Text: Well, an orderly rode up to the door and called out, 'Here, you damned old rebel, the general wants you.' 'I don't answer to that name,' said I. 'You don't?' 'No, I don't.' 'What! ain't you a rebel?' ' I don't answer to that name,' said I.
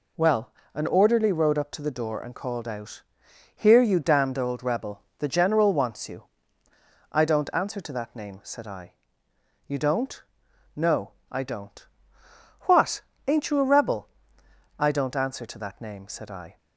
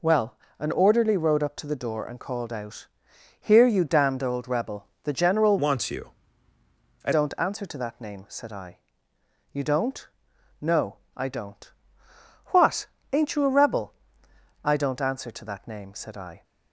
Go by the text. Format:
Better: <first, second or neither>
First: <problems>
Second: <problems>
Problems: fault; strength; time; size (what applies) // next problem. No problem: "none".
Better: first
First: none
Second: changes voice from "wants" to "I"; from 5.5 to 7.1 s; 1.6 s long